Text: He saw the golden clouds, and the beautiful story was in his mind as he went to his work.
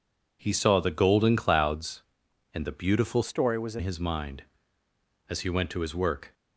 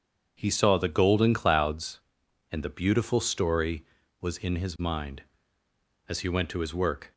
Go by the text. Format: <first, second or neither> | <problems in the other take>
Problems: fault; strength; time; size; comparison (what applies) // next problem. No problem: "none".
second | changes voice from "story" to "in"; from 3.2 to 3.8 s; 0.6 s long